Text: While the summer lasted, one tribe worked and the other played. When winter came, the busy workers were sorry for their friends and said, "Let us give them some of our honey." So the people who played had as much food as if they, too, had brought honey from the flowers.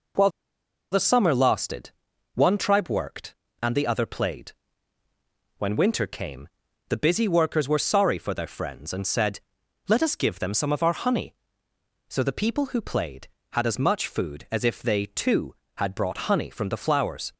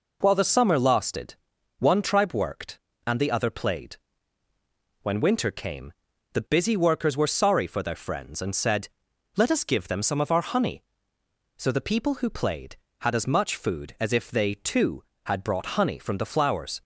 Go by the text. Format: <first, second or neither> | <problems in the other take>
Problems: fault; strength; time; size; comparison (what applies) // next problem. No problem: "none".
second | pauses between "While" and "the"; noticeable; at 0.3 s; 0.61 s long